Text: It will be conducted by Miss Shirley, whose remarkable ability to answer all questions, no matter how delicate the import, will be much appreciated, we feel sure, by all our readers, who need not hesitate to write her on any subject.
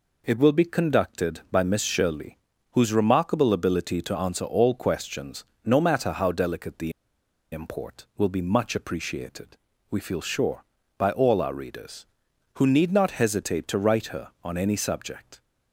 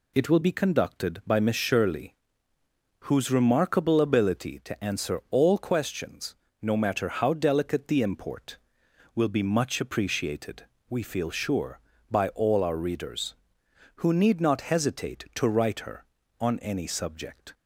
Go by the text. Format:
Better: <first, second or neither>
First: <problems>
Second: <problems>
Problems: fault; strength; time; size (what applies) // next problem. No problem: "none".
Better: second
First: pauses between "the" and "import"; noticeable; at 6.9 s; 0.60 s long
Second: none